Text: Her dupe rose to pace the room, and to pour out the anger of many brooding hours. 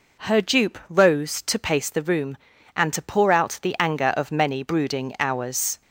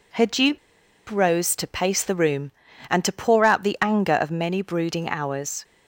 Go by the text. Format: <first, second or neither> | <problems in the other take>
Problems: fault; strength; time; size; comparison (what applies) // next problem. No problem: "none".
first | pauses between "dupe" and "rose"; noticeable; at 0.5 s; 0.50 s long